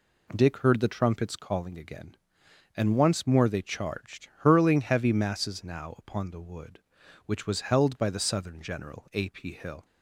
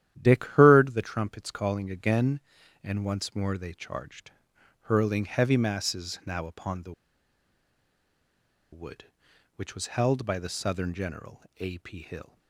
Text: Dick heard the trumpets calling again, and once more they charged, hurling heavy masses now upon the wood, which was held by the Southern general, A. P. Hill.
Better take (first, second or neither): first